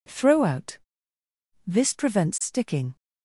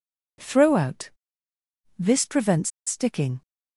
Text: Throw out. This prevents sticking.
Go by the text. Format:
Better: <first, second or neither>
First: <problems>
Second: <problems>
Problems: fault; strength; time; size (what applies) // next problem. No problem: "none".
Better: first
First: none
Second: pauses between "prevents" and "sticking"; slight; at 2.6 s; 0.17 s long